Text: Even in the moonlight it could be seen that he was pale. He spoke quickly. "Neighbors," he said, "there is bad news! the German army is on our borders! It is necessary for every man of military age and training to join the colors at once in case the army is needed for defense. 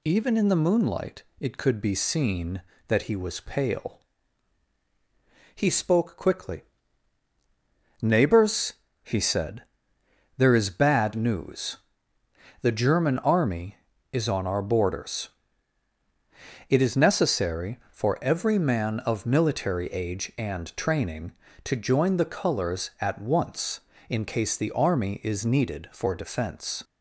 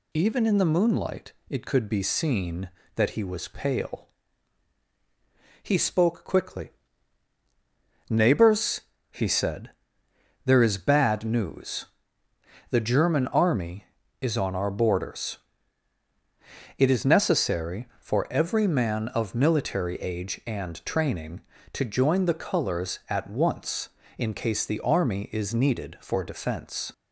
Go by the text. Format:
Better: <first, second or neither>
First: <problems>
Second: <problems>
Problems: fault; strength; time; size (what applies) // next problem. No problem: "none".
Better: neither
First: pauses between "moonlight" and "it"; slight; at 1.2 s; 0.18 s long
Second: pauses between "moonlight" and "it"; slight; at 1.3 s; 0.18 s long